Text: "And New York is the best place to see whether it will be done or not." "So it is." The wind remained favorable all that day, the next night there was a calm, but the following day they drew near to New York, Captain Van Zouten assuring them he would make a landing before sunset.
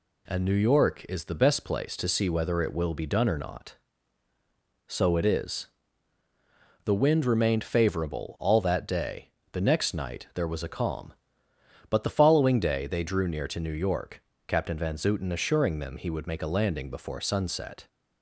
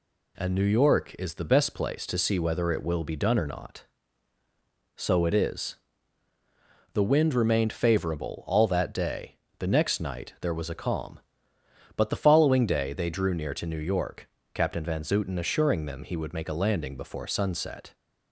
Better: neither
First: none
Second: none

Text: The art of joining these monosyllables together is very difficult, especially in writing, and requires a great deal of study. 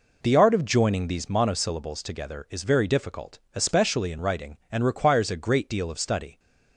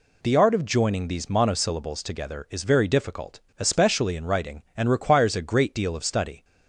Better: second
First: starts louder than the rest; noticeable; until 1.4 s; 4 dB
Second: none

